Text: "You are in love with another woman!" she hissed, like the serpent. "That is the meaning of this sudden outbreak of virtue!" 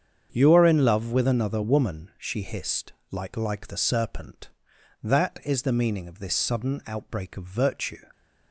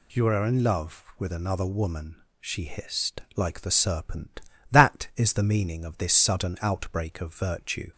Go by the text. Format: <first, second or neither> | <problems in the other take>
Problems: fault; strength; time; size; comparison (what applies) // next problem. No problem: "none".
second | starts louder than the rest; strong; until 1.3 s; 7.5 dB // says "like" twice; at 3.3 s